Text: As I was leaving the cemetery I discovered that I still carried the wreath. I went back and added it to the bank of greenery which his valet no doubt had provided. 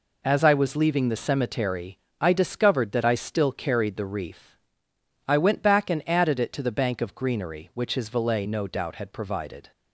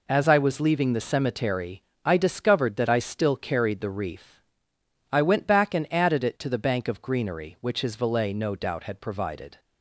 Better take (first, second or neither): neither